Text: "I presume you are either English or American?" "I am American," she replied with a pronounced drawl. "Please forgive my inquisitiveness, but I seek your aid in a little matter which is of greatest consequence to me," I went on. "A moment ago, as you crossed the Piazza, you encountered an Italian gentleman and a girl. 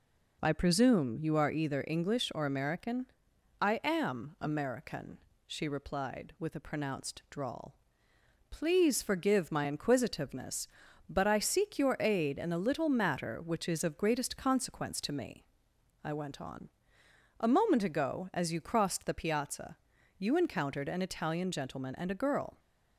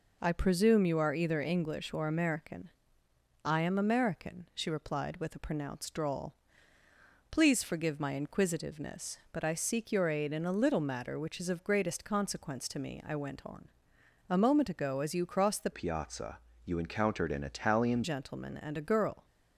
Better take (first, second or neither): first